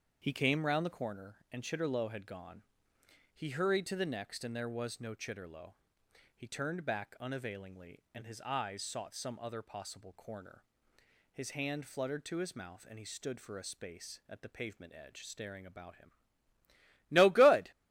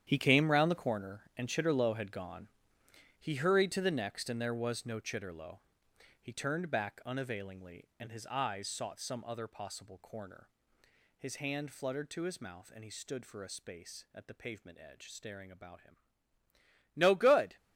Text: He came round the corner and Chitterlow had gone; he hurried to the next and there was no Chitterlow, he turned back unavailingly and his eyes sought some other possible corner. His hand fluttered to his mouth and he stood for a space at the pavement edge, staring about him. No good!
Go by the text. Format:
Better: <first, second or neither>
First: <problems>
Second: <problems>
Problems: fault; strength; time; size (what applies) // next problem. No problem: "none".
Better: first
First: starts louder than the rest; until 1.2 s; 7 dB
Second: gets quieter; strong; throughout; 13.5 dB // starts louder than the rest; strong; until 1.0 s; 9.5 dB